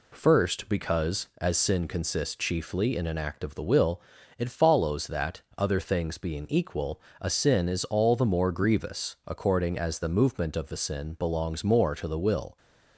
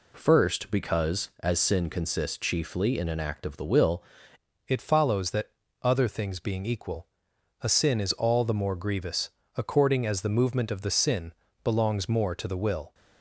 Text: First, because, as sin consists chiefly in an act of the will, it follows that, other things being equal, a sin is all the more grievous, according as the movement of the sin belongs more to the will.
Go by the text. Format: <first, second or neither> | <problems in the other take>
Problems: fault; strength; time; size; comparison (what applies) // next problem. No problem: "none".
first | changes voice at "it"; from 4.6 s on; 8.3 s long // pauses between "sin" and "belongs"; slight; at 11.3 s; 0.30 s long